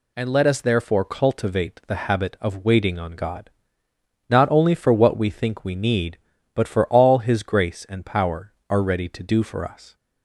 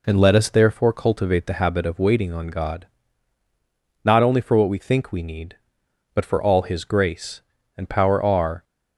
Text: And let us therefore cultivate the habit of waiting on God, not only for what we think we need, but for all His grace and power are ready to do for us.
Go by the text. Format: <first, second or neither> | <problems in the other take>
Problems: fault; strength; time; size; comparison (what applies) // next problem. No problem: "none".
first | stops before "ready to do for us"; at 8.6 s